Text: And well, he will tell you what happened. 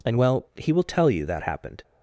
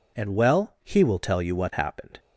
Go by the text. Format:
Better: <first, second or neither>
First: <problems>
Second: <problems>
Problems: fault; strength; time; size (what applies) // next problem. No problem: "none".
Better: second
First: says "that" for "what"; at 1.2 s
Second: none